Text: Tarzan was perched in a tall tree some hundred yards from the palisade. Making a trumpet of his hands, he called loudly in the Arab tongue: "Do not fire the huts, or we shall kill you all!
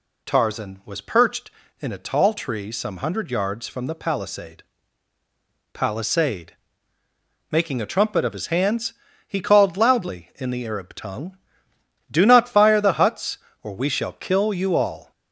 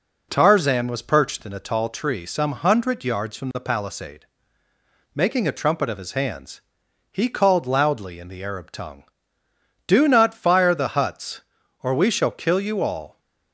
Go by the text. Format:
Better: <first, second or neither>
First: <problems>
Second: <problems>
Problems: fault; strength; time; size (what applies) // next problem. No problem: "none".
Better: second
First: says "palisade" twice; at 5.7 s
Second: none